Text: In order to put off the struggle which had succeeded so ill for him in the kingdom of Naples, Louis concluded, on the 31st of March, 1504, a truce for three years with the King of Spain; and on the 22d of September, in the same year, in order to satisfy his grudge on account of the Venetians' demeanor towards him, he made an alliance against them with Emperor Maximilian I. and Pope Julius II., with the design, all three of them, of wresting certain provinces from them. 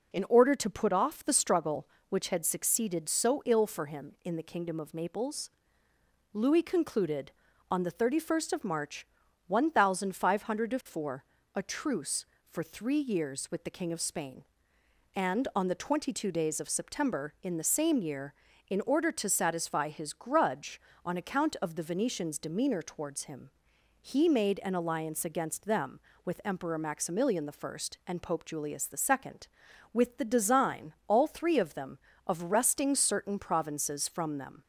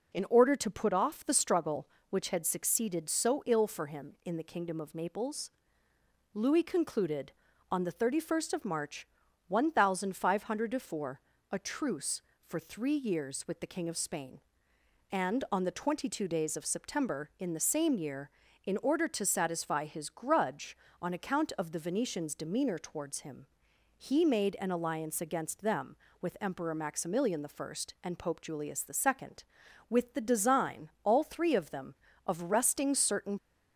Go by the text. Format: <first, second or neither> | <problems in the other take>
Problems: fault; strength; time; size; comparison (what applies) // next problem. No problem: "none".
first | stops before "provinces from them"; at 33.3 s